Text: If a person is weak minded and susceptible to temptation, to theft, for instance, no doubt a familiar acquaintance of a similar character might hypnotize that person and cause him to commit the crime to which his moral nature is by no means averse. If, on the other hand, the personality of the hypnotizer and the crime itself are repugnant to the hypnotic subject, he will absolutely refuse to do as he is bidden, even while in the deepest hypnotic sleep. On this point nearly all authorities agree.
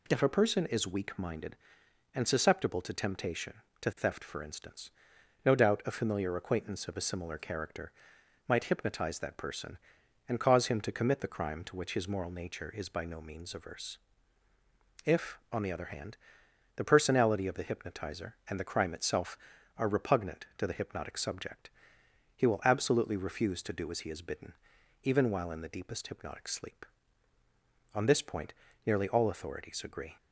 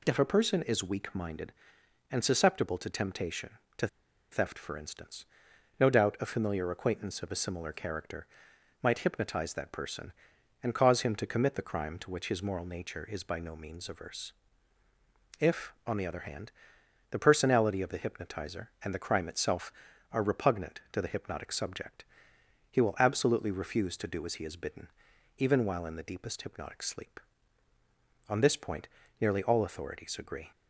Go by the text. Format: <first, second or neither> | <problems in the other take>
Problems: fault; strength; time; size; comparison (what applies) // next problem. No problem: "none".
first | pauses between "to" and "theft"; at 3.8 s; 0.44 s long // pauses between "character" and "might"; noticeable; at 8.2 s; 0.56 s long; noticeable in the first // pauses between "point" and "nearly"; slight; at 28.8 s; 0.34 s long; slight in the first